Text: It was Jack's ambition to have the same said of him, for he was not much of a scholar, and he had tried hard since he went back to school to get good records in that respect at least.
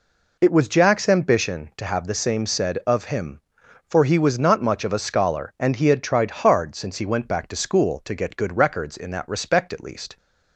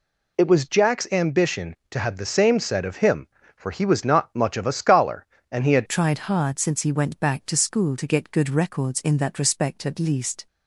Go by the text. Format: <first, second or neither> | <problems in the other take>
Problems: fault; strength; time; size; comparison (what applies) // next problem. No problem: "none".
first | changes voice at "tried"; from 5.8 s on; 4.6 s long